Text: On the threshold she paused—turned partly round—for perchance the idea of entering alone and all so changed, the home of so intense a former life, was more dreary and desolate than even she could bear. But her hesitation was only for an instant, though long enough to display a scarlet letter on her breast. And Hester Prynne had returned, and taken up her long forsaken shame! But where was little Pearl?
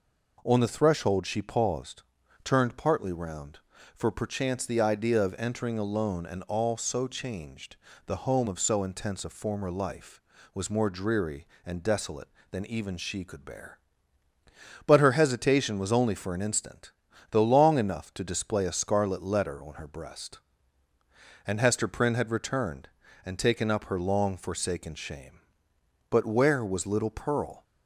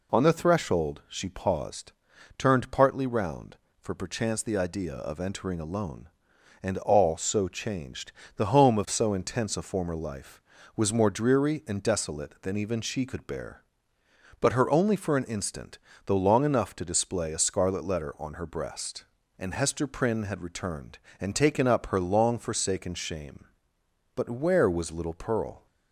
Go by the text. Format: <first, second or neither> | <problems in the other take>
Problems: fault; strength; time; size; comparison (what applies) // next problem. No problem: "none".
first | skips "hesitation was"; at 14.7 s